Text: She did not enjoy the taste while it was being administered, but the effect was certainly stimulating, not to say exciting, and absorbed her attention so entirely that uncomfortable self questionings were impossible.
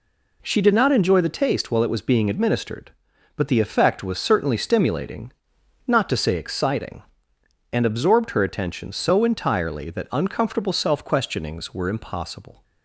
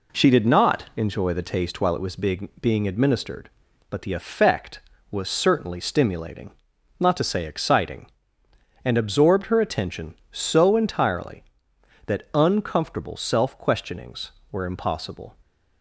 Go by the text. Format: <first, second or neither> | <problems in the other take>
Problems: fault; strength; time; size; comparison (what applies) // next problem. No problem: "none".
first | says "being" twice; at 2.5 s